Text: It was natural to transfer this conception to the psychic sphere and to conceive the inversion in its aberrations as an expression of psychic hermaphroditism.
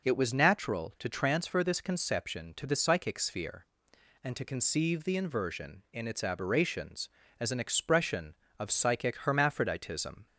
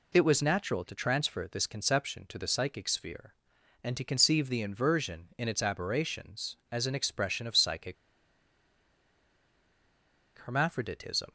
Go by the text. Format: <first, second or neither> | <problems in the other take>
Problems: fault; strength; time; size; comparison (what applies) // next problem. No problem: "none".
first | pauses between "psychic" and "hermaphroditism"; strong; at 7.9 s; 2.4 s long